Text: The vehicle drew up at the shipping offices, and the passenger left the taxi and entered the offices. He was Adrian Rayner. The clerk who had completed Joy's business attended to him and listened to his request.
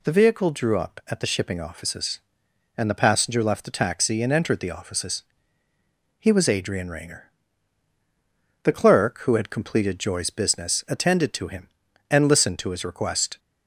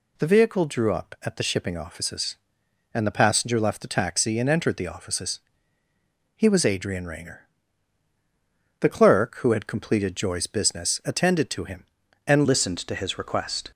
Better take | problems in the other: first | changes voice at "listened"; from 12.4 s on; 1.3 s long

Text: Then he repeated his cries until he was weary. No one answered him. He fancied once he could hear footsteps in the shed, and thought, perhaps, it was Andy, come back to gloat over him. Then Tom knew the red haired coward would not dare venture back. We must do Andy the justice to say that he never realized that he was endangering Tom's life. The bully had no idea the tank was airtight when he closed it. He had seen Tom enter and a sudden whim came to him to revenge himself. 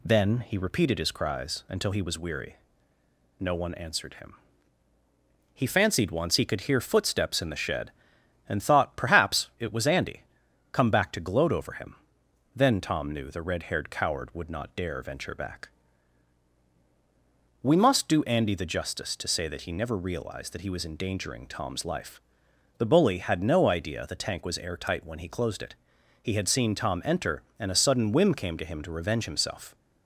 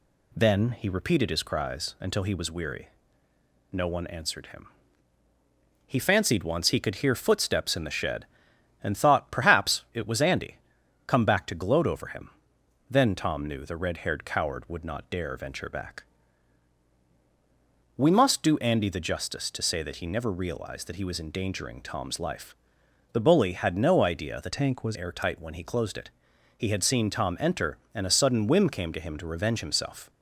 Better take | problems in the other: first | changes voice from "tank" to "was"; from 24.5 to 24.9 s; 0.4 s long

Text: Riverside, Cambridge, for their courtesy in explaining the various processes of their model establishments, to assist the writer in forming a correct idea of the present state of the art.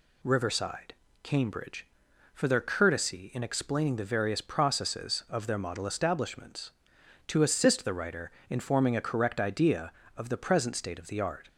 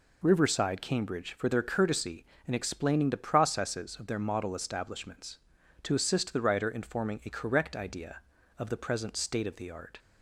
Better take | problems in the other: first | skips "various"; at 3.1 s

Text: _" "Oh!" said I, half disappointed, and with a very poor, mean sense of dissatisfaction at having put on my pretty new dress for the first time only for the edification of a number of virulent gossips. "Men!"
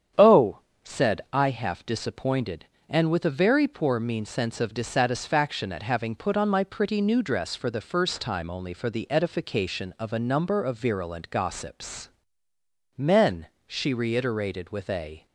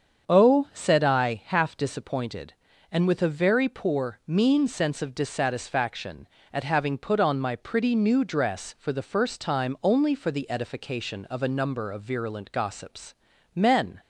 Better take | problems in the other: second | starts louder than the rest; strong; until 1.5 s; 8.5 dB; strong in the second // goes on to say "she reiterated with a"; from 13.6 s on; 1.6 s long

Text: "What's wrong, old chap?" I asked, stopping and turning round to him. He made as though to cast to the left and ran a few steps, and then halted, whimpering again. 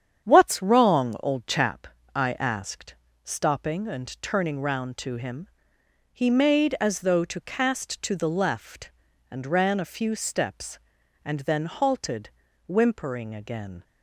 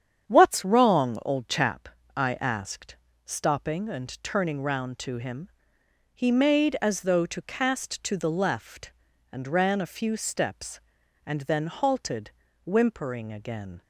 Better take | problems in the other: neither | starts louder than the rest; strong; the same in both

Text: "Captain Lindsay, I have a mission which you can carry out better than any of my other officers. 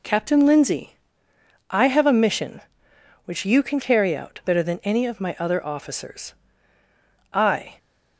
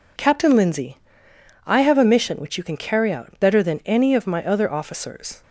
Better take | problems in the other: second | goes on to say "I"; slight; from 7.3 s on; 0.46 s long

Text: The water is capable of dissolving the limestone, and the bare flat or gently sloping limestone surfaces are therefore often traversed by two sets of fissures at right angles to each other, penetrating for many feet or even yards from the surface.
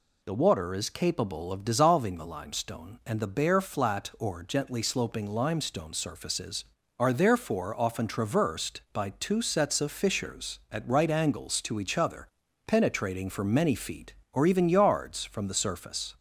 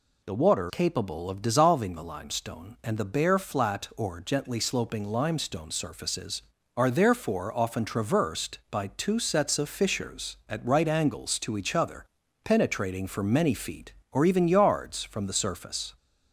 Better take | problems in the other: first | skips "is"; at 0.6 s

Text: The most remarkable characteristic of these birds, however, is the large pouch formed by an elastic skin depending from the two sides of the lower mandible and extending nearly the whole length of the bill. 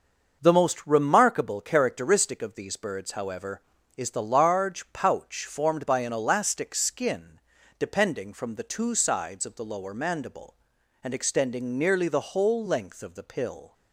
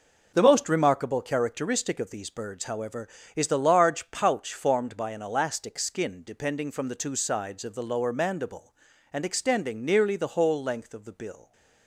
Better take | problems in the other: second | starts louder than the rest; noticeable; until 1.4 s; 6 dB // pauses between "skin" and "depending"; at 7.3 s; 0.40 s long // says "pill" for "bill"; at 13.2 s

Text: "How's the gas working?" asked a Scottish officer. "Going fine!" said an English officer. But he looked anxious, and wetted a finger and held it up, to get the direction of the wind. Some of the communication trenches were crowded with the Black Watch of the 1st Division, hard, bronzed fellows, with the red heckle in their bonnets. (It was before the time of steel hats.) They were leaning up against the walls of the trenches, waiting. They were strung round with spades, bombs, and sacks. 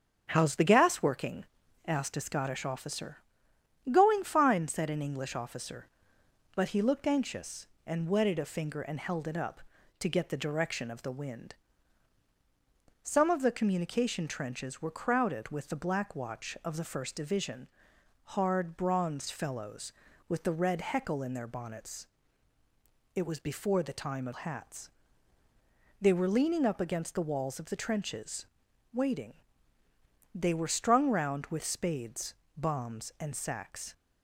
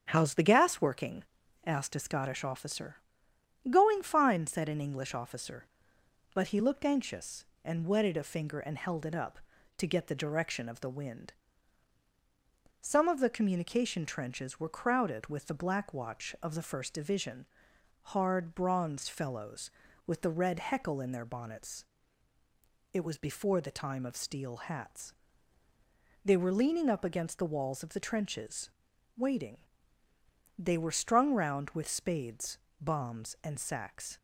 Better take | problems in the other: second | starts louder than the rest; strong; until 1.3 s; 8.5 dB; strong in the second // skips "steel"; at 24.3 s

